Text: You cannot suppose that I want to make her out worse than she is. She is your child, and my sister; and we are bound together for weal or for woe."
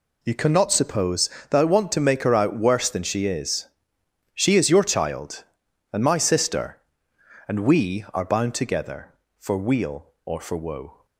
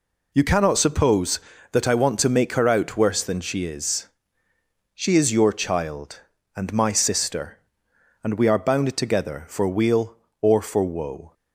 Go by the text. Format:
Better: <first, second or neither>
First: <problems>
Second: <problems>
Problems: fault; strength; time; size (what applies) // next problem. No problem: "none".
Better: neither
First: none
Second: none